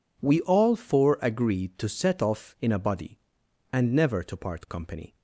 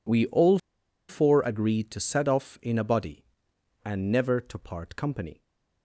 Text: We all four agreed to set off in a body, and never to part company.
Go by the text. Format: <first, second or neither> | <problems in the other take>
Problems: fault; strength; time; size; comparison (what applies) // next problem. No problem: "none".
first | pauses between "all" and "four"; noticeable; at 0.5 s; 0.51 s long